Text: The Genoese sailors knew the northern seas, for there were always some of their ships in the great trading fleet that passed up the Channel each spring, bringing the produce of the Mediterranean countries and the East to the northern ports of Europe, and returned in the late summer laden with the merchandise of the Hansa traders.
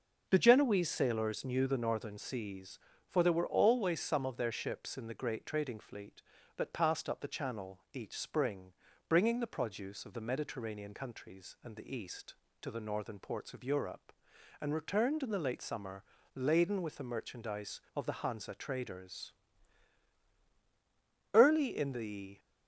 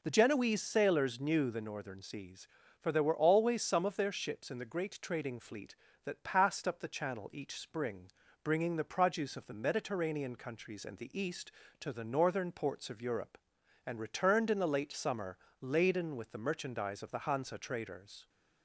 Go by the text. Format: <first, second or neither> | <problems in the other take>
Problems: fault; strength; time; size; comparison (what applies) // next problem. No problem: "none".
second | pauses between "summer" and "laden"; slight; at 16.0 s; 0.34 s long; slight in the second // goes on to say "Early in the"; noticeable; from 21.3 s on; 1.0 s long